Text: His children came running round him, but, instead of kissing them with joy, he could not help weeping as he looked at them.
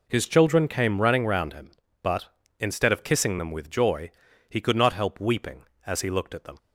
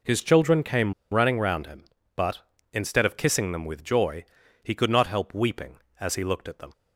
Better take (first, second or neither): first